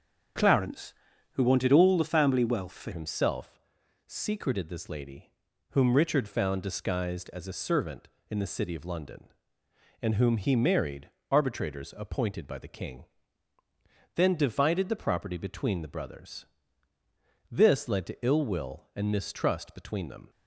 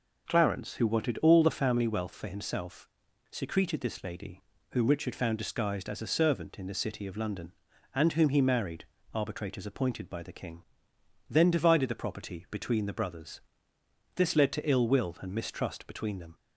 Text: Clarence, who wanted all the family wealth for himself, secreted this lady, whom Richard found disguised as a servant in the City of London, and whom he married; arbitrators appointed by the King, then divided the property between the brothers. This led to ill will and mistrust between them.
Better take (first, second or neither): second